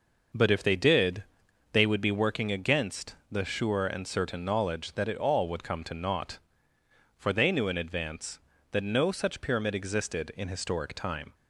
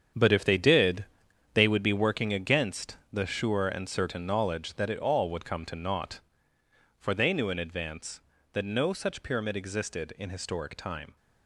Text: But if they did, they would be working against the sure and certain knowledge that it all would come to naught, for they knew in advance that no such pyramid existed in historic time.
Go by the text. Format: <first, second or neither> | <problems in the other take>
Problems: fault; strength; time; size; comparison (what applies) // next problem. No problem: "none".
first | gets quieter; strong; throughout; 10.5 dB